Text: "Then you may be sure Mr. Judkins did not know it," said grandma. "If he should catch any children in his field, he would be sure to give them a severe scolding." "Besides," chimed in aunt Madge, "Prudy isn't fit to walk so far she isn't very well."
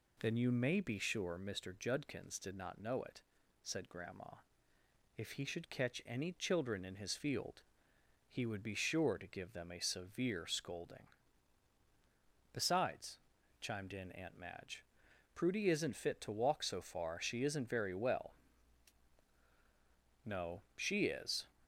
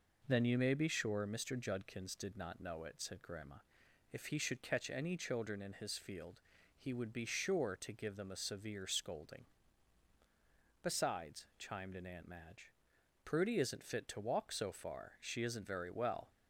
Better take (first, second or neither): second